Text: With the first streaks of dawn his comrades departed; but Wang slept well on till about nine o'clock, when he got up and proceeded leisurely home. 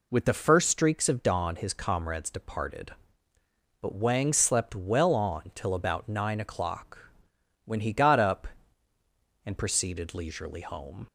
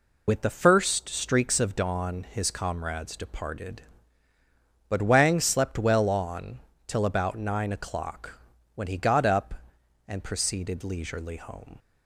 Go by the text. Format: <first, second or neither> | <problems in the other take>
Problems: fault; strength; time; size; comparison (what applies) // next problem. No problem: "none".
first | loses the start of "With"; at 0.2 s; 65 ms // pauses between "on" and "till"; slight; at 6.5 s; 0.28 s long